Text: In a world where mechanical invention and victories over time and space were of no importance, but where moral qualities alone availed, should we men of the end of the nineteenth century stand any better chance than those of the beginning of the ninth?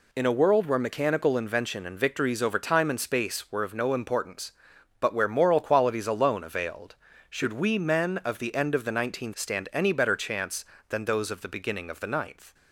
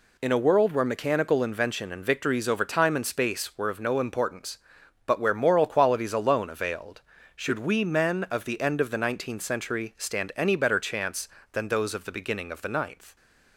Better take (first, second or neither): second